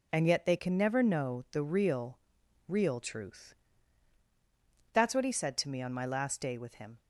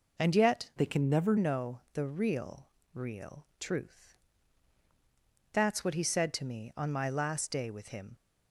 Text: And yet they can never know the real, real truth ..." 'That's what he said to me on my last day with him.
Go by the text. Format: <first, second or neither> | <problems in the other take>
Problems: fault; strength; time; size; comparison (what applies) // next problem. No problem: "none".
first | changes voice from "they" to "never"; from 0.7 to 1.3 s; 0.6 s long